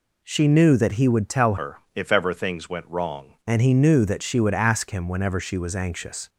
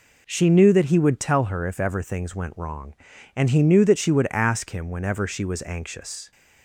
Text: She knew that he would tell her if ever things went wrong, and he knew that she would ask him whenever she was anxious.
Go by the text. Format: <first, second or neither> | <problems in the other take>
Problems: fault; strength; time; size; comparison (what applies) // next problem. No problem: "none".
second | changes voice from "her" to "wrong"; from 1.5 to 3.3 s; 1.8 s long // pauses between "her" and "if"; slight; at 1.7 s; 0.16 s long